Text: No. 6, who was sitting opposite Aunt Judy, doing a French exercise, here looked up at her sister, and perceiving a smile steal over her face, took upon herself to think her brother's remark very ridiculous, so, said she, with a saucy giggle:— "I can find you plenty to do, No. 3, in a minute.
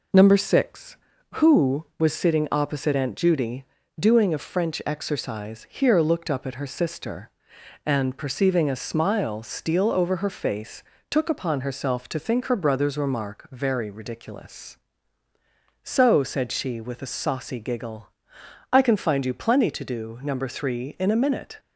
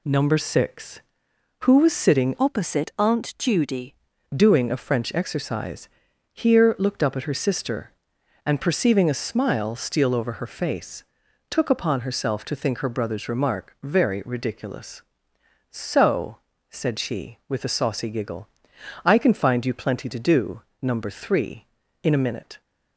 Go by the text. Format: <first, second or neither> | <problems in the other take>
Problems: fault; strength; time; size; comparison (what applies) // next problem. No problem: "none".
first | changes voice from "opposite" to "Judy"; from 2.3 to 3.9 s; 1.6 s long